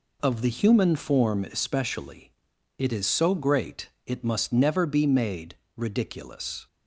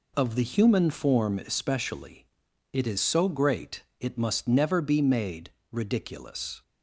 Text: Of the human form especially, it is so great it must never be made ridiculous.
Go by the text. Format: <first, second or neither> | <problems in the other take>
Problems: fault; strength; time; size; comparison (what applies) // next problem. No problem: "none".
neither | pauses between "great" and "it"; slight; the same in both // pauses between "made" and "ridiculous"; slight; the same in both